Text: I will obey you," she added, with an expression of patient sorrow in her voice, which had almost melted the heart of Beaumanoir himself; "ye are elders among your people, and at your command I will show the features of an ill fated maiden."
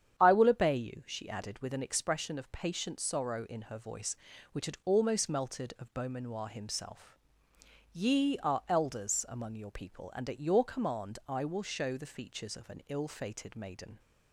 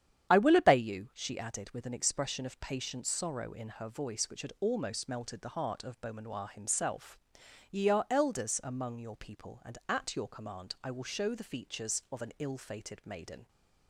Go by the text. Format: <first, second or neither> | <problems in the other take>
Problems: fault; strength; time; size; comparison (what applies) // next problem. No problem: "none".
second | starts louder than the rest; strong; until 1.2 s; 9 dB; strong in the second // skips "the heart"; at 5.7 s